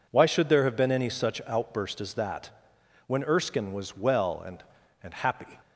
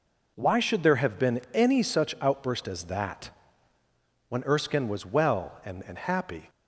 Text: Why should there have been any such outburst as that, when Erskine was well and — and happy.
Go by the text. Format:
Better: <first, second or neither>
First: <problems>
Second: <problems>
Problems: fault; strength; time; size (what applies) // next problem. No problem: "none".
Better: neither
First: none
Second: none